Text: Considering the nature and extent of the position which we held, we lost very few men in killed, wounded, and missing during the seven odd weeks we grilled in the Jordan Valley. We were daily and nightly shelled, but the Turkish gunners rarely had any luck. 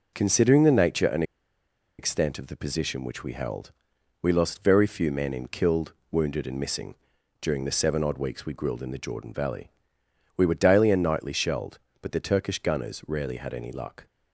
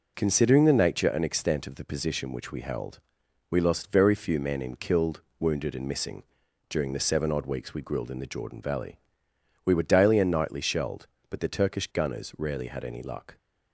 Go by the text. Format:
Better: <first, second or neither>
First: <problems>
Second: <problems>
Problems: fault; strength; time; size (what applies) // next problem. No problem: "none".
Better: second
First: pauses between "and" and "extent"; noticeable; at 1.2 s; 0.75 s long // pauses between "missing" and "during"; noticeable; at 6.9 s; 0.46 s long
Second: pauses between "missing" and "during"; noticeable; at 6.2 s; 0.46 s long